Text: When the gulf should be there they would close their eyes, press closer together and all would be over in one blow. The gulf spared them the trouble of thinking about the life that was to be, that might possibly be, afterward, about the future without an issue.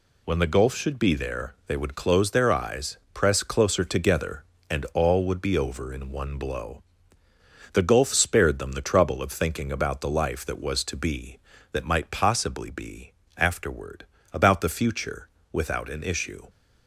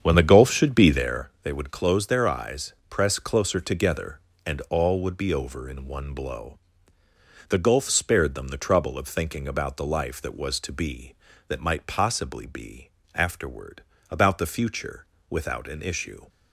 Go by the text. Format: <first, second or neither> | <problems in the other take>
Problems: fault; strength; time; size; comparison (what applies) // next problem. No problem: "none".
first | starts louder than the rest; strong; until 1.3 s; 8 dB // pauses between "future" and "without"; slight; at 15.0 s; 0.24 s long; slight in the first